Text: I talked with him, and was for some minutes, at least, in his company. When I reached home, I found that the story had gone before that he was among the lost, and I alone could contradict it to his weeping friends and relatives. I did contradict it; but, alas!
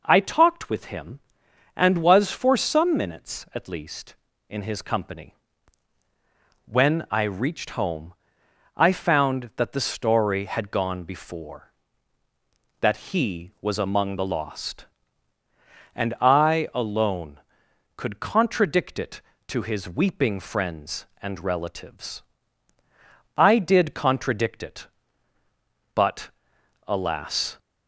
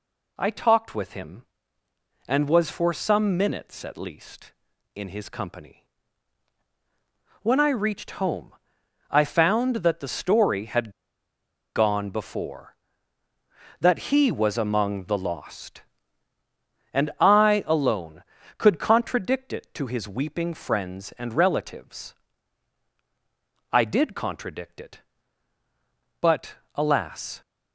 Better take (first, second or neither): first